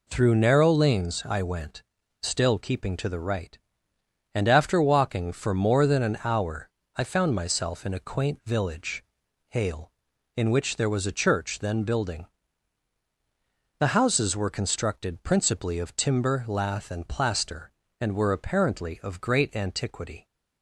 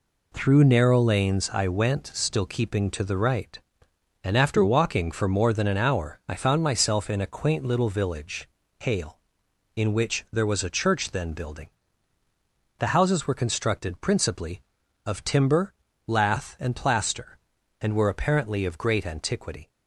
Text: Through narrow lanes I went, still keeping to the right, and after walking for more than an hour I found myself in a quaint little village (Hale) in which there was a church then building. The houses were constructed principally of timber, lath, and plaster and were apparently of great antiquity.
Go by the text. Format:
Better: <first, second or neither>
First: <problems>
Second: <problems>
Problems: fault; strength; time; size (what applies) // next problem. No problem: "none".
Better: second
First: pauses between "hour" and "I"; slight; at 6.6 s; 0.26 s long // skips "little"; at 8.4 s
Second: none